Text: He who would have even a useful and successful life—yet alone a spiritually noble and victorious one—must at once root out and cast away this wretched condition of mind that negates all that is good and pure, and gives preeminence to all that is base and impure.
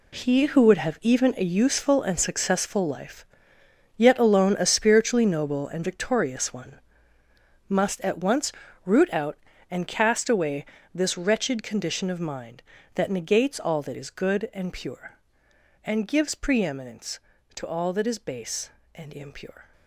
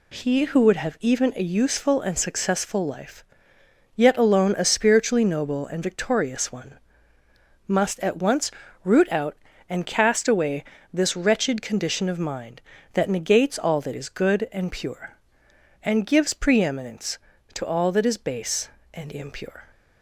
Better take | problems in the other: second | gets quieter; strong; throughout; 11 dB // pauses between "once" and "root"; slight; at 8.5 s; 0.34 s long; slight in the second // pauses between "away" and "this"; slight; at 10.6 s; 0.28 s long; slight in the second

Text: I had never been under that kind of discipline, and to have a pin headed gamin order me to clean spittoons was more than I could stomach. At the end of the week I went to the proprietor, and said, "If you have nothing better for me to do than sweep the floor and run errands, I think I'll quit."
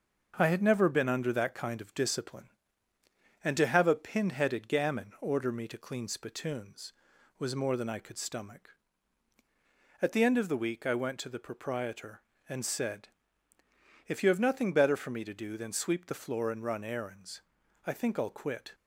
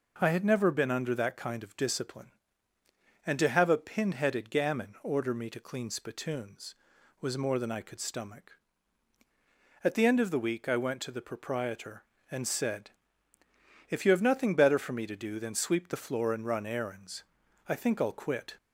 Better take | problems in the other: second | gets quieter; throughout; 3.5 dB

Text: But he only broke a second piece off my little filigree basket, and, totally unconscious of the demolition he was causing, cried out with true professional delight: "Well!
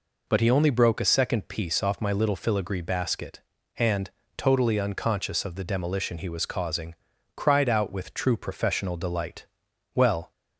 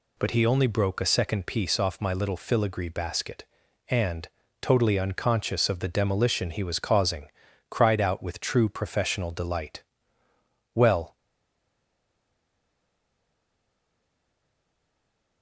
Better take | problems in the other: first | stays silent after the last word; strong; from 11.1 s on; 4.3 s long

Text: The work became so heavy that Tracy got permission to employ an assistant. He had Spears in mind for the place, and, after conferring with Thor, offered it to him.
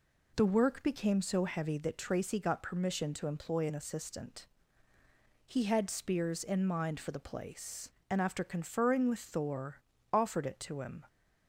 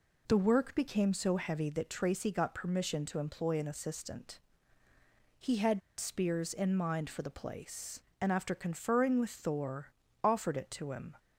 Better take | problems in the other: first | pauses between "had" and "Spears"; slight; at 5.8 s; 0.18 s long

